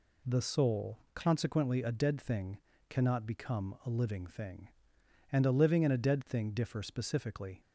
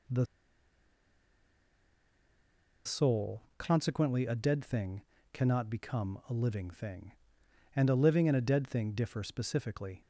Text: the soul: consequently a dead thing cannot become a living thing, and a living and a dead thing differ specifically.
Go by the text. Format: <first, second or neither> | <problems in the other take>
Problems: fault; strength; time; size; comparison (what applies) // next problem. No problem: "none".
first | pauses between "the" and "soul"; strong; at 0.2 s; 2.5 s long // pauses between "thing" and "cannot"; slight; at 5.0 s; 0.30 s long; slight in the first